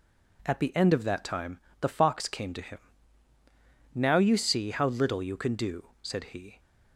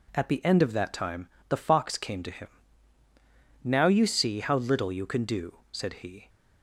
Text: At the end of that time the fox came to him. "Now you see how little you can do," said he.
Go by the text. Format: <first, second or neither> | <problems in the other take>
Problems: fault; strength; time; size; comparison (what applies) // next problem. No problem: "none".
neither | pauses between "time" and "the"; slight; the same in both